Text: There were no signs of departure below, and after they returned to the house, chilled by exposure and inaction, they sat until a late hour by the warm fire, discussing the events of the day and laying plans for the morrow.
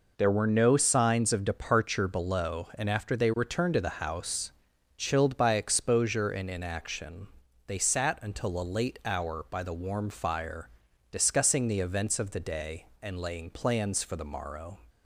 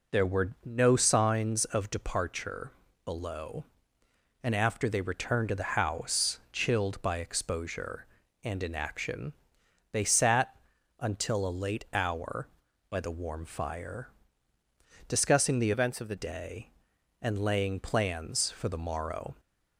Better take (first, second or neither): first